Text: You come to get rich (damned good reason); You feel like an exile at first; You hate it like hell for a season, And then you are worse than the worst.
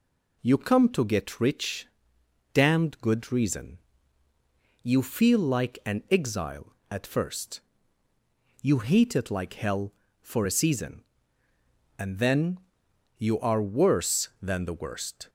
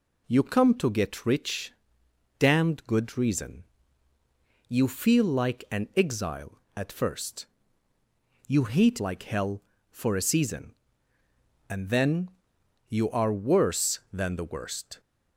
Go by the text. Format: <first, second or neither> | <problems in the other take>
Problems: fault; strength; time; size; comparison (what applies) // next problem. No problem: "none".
first | skips "it"; at 8.9 s // pauses between "then" and "you"; noticeable; at 12.2 s; 0.58 s long; noticeable in the first